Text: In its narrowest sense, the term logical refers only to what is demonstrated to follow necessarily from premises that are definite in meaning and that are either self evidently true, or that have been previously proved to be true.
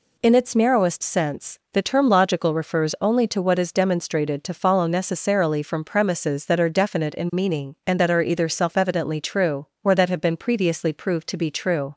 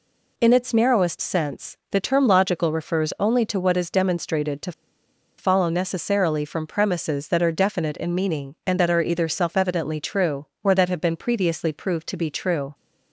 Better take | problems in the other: first | pauses between "to" and "follow"; noticeable; at 4.7 s; 0.66 s long

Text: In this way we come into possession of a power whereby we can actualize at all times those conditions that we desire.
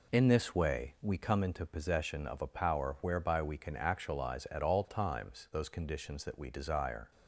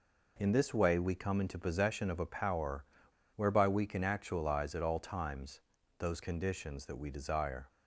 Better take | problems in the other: first | pauses between "power" and "whereby"; noticeable; at 2.8 s; 0.49 s long // pauses between "times" and "those"; at 5.6 s; 0.38 s long

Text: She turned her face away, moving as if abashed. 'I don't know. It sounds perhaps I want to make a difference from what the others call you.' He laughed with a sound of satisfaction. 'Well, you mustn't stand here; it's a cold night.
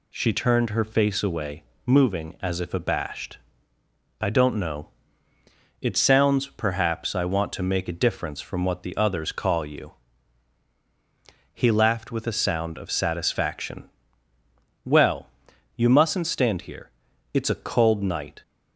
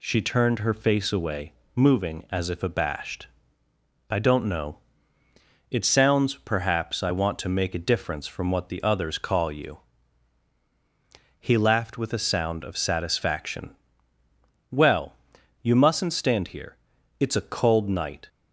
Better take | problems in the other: neither | none

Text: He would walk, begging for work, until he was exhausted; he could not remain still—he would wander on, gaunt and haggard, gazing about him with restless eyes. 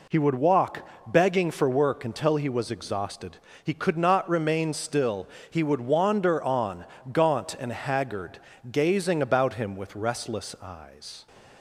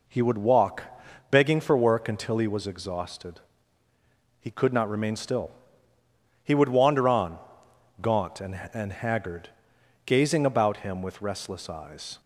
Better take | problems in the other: first | says "and" twice; at 8.7 s

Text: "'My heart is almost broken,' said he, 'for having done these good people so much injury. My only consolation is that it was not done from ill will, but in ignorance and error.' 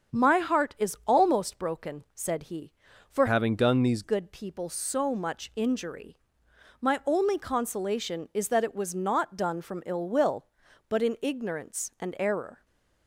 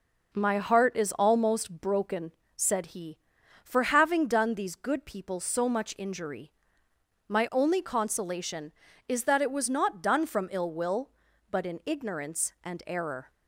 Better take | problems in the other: second | starts louder than the rest; strong; until 1.2 s; 7.5 dB // changes voice from "having" to "these"; from 3.2 to 4.0 s; 0.8 s long // stays silent after the last word; slight; from 12.5 s on; 0.5 s long

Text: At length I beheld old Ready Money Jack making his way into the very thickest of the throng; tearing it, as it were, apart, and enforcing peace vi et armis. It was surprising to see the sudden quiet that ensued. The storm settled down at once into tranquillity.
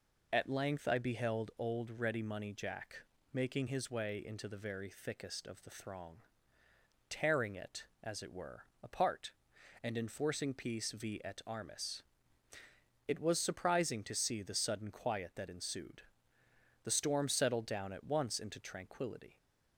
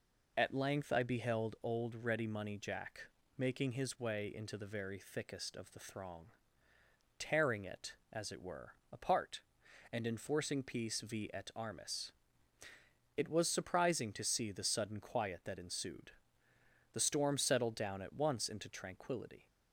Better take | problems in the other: neither | pauses between "Jack" and "making"; slight; the same in both

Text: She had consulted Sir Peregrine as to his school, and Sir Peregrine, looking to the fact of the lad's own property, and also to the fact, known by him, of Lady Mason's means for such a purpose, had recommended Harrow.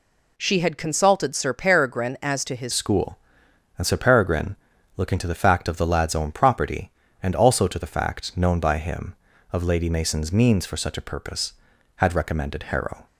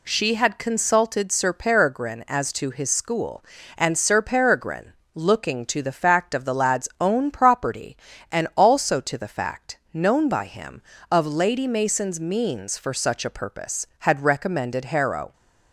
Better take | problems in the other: second | changes voice at "school"; from 2.7 s on; 10.3 s long

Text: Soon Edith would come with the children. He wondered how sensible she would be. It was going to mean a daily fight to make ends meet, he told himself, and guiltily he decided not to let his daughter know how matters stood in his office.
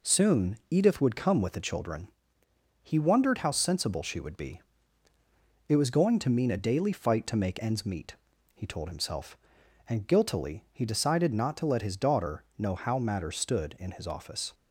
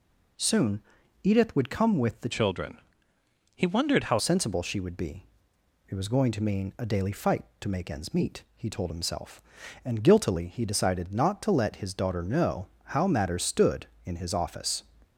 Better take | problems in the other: first | pauses between "Soon" and "Edith"; at 0.8 s; 0.42 s long // changes voice from "children" to "how"; from 2.3 to 4.1 s; 1.8 s long // pauses between "know" and "how"; slight; at 12.6 s; 0.20 s long

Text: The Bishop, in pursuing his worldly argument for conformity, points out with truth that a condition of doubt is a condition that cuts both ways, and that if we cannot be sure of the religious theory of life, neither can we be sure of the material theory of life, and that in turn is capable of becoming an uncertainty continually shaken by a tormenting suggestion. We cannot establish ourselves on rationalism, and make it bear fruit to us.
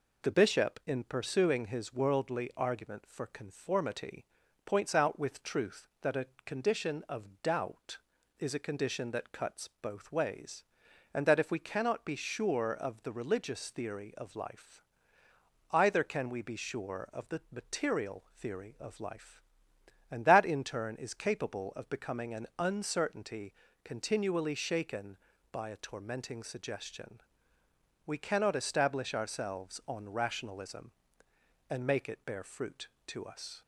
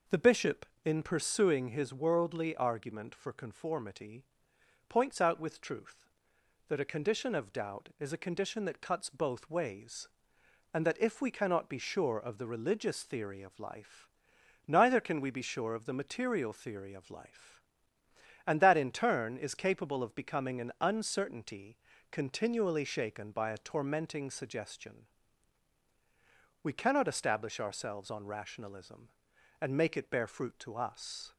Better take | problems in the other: second | pauses between "a" and "condition"; slight; at 6.2 s; 0.18 s long // says "either" for "neither"; at 15.7 s // pauses between "uncertainty" and "continually"; slight; at 23.5 s; 0.30 s long; slight in the second

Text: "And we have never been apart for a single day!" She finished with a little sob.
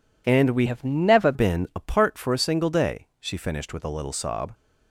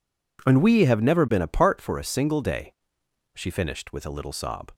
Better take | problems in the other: second | changes voice from "have" to "never"; from 0.6 to 1.3 s; 0.7 s long

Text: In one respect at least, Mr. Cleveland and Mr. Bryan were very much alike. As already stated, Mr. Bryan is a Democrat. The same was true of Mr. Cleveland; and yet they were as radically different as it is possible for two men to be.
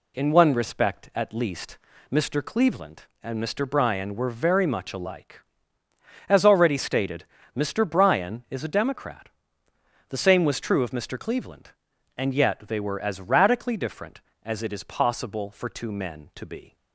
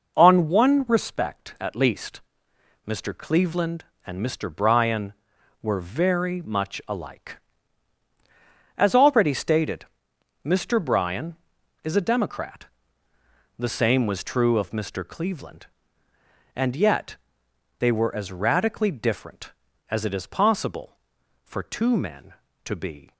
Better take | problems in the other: first | says "On" for "In"; at 0.1 s // pauses between "yet" and "they"; noticeable; at 17.1 s; 0.62 s long

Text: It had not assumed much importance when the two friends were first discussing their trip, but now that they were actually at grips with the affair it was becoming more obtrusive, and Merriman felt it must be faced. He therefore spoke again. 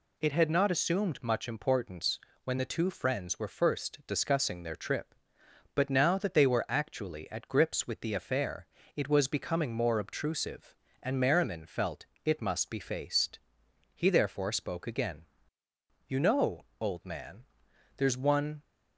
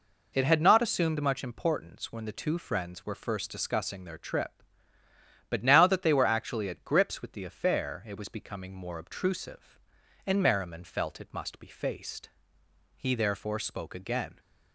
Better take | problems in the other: second | pauses between "importance" and "when"; slight; at 2.1 s; 0.26 s long // pauses between "affair" and "it"; slight; at 8.6 s; 0.28 s long // pauses between "felt" and "it"; slight; at 12.0 s; 0.18 s long // goes on to say "You know old man there's one"; strong; from 16.0 s on; 2.5 s long

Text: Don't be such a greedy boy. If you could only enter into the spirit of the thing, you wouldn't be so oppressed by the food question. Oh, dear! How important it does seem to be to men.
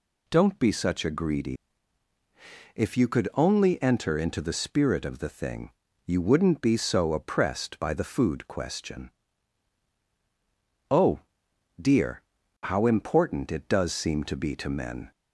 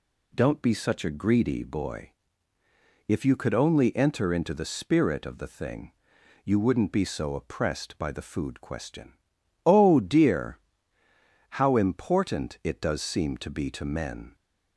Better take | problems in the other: second | skips "boy"; at 2.1 s

